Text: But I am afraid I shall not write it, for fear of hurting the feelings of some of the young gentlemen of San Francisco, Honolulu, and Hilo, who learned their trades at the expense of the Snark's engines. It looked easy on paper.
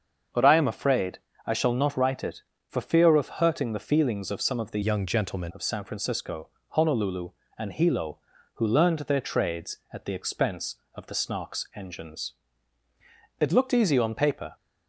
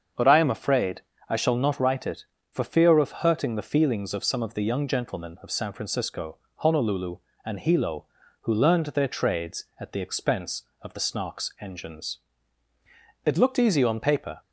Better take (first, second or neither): second